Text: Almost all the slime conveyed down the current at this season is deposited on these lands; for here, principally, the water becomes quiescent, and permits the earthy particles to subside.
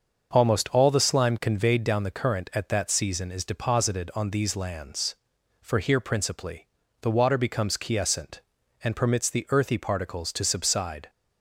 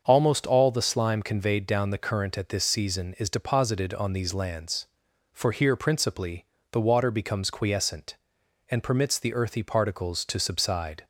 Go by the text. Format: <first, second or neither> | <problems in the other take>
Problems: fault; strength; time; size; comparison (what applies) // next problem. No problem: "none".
second | starts louder than the rest; until 1.3 s; 6.5 dB; also in the second // says "that" for "this"; at 2.6 s